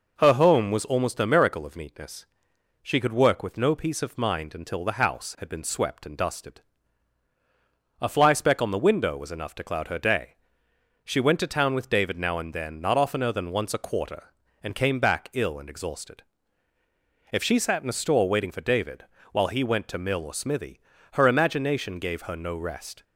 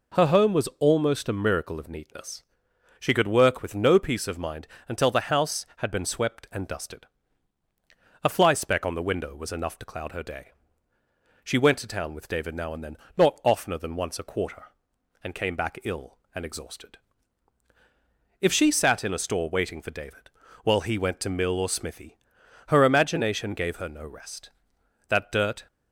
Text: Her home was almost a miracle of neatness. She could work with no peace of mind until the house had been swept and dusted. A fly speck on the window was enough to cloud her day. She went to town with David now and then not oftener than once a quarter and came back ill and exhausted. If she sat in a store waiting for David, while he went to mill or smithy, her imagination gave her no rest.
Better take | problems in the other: first | pauses between "mind" and "until"; slight; at 4.6 s; 0.20 s long // pauses between "then" and "not"; slight; at 12.9 s; 0.20 s long // goes on to say "That dirt"; from 25.0 s on; 0.60 s long

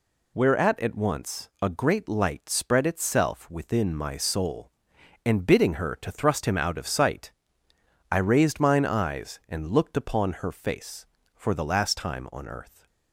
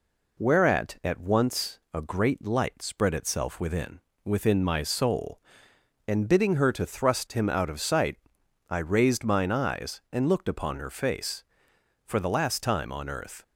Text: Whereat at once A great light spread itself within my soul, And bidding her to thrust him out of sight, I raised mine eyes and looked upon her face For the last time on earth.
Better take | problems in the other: first | says "within" twice; at 4.2 s

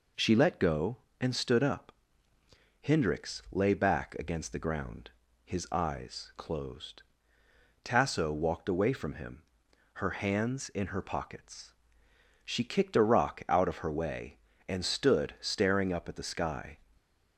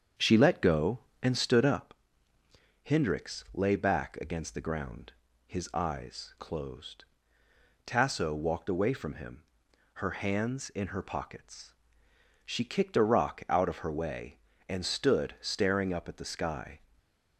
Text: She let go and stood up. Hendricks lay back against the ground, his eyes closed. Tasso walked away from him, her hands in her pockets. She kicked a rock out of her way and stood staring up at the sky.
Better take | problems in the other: first | starts louder than the rest; strong; until 1.9 s; 7.5 dB // stays silent after the last word; slight; from 16.7 s on; 0.6 s long; slight in the first

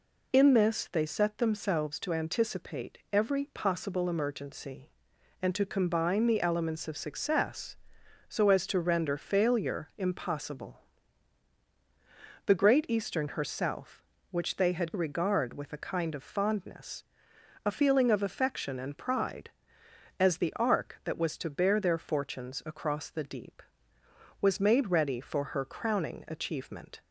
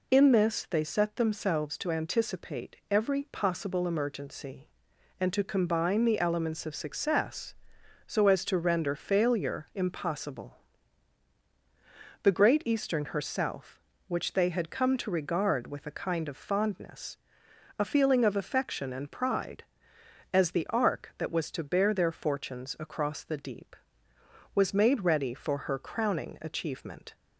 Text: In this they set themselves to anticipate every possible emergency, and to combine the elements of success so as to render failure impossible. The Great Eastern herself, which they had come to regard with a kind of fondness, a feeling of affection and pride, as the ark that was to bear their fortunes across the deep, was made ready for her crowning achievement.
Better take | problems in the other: second | pauses between "anticipate" and "every"; slight; at 2.9 s; 0.16 s long; slight in the second // skips "come to"; at 14.9 s

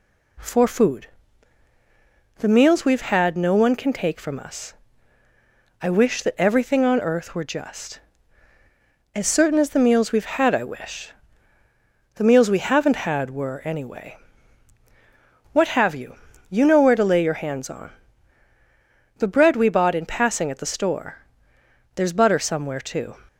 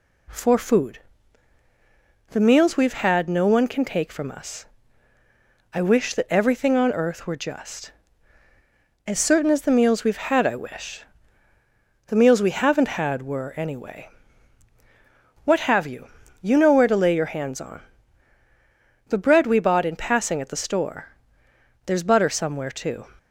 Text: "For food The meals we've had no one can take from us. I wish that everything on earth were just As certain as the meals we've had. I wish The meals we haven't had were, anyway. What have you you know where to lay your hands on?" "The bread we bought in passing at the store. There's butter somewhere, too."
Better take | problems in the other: neither | pauses between "food" and "The"; strong; the same in both // pauses between "wish" and "The"; the same in both // pauses between "you" and "you"; slight; the same in both

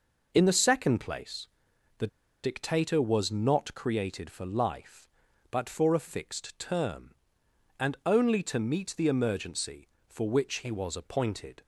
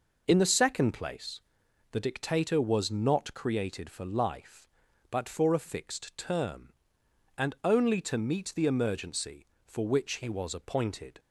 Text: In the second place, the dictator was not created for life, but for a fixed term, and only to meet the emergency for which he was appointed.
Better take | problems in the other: second | pauses between "the" and "dictator"; slight; at 2.0 s; 0.35 s long

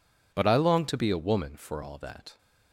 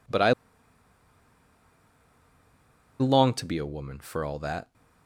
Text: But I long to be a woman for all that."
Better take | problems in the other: first | pauses between "I" and "long"; strong; at 0.3 s; 2.6 s long

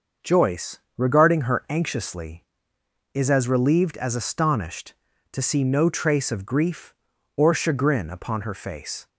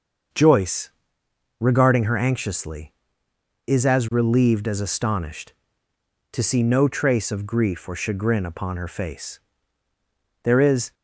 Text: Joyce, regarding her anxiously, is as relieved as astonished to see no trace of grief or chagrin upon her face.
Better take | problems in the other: first | starts louder than the rest; until 2.0 s; 6.5 dB; also in the first // goes on to say "There is"; from 10.4 s on; 0.52 s long

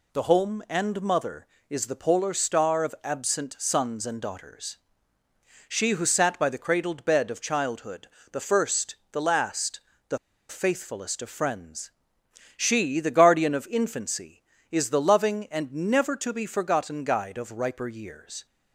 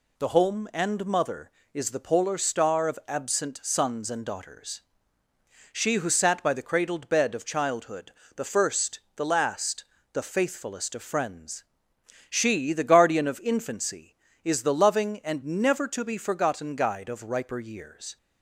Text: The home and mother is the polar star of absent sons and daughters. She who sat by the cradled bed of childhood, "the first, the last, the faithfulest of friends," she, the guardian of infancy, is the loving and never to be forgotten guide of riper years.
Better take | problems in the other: second | pauses between "the" and "faithfulest"; slight; at 10.1 s; 0.31 s long

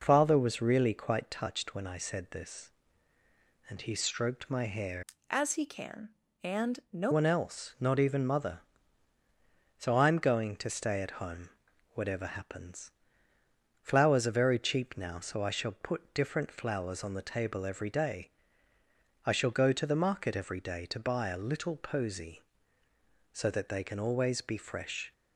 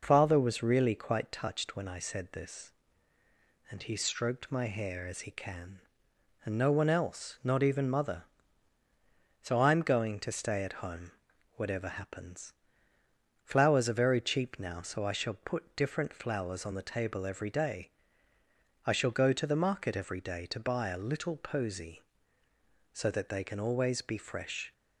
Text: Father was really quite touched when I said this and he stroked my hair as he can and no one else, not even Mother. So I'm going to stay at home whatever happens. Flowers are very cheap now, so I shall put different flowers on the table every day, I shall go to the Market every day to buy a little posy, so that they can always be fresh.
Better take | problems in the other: second | changes voice from "as" to "no"; from 5.3 to 7.1 s; 1.8 s long // pauses between "home" and "whatever"; at 11.4 s; 0.42 s long; also in the second

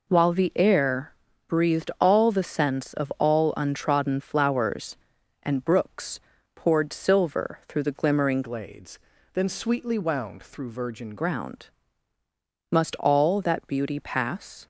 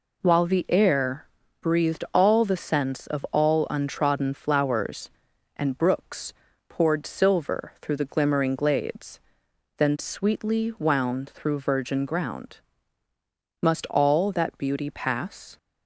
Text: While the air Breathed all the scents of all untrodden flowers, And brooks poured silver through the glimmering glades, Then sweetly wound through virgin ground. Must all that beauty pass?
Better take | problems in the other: second | pauses between "air" and "Breathed"; slight; at 1.1 s; 0.36 s long; slight in the second // pauses between "brooks" and "poured"; slight; at 6.1 s; 0.36 s long; slight in the second // changes voice from "glades" to "virgin"; from 8.4 to 11.1 s; 2.7 s long

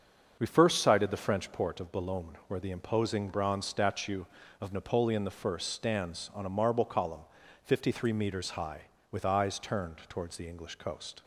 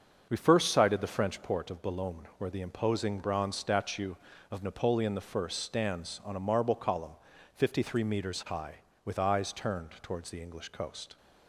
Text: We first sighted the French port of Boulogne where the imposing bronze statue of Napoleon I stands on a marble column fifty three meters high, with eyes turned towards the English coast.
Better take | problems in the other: neither | starts louder than the rest; the same in both // pauses between "column" and "fifty"; slight; the same in both

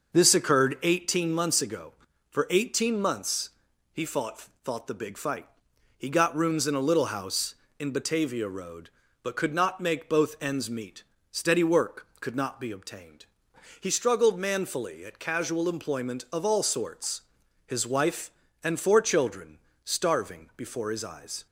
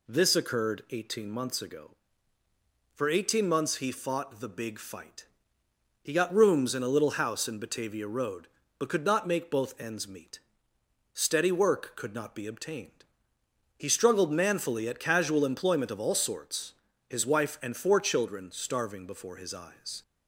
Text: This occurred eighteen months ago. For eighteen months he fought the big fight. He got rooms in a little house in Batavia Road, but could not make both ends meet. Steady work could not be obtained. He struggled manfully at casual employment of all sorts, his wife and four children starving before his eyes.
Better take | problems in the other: second | starts louder than the rest; noticeable; until 1.1 s; 6 dB // pauses between "months" and "he"; noticeable; at 3.4 s; 0.46 s long // says "fought" twice; at 4.6 s // pauses between "children" and "starving"; slight; at 19.6 s; 0.22 s long

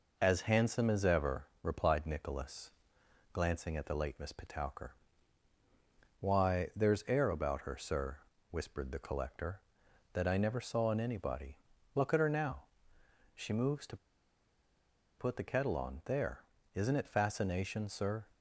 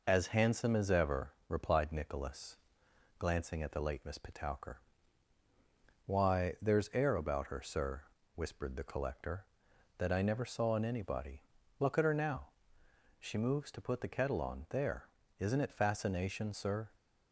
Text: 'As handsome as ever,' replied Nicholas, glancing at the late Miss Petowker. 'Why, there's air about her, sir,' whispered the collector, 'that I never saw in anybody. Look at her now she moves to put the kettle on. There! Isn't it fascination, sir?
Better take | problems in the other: second | pauses between "now" and "she"; noticeable; at 12.6 s; 0.70 s long; noticeable in the second // pauses between "to" and "put"; at 13.9 s; 1.2 s long

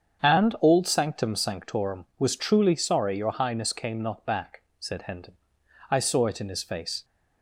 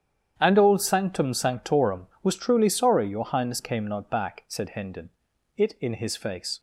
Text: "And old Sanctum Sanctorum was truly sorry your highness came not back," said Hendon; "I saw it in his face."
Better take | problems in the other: first | starts louder than the rest; strong; until 1.3 s; 9 dB; strong in the first // skips "I saw"; at 5.3 s

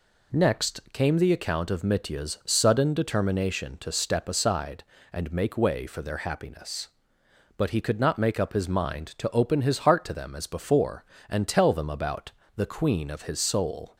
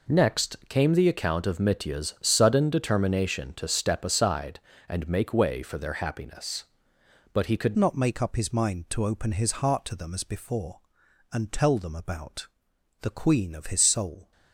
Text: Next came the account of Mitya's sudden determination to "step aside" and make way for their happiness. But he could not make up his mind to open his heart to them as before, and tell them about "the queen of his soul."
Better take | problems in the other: first | changes voice at "not"; from 7.7 s on; 6.6 s long // pauses between "about" and "the"; noticeable; at 12.4 s; 0.54 s long; slight in the first

